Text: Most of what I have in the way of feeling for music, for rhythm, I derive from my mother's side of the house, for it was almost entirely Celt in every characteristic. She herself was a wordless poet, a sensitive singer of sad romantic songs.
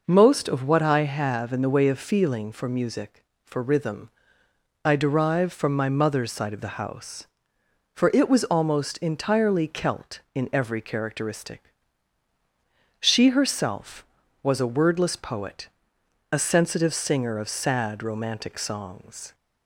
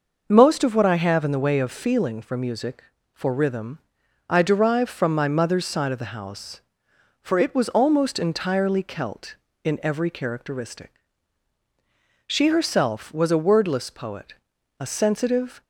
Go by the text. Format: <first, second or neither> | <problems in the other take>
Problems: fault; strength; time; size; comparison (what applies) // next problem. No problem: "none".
first | stops before "singer of sad romantic songs"; at 15.6 s